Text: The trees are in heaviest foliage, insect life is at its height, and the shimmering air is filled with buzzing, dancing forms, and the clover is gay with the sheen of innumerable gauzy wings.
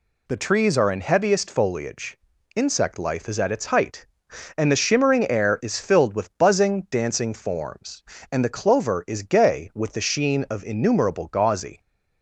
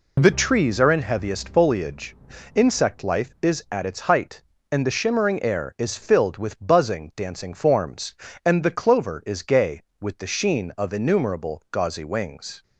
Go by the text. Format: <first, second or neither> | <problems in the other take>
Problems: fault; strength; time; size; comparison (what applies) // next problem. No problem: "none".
second | stops before "wings"; at 11.8 s